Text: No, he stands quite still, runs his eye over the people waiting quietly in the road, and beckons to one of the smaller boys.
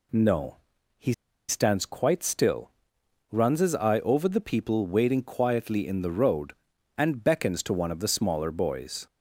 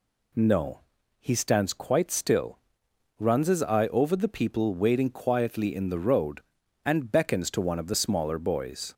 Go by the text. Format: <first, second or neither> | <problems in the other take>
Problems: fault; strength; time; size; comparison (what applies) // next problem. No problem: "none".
second | pauses between "he" and "stands"; at 1.1 s; 0.36 s long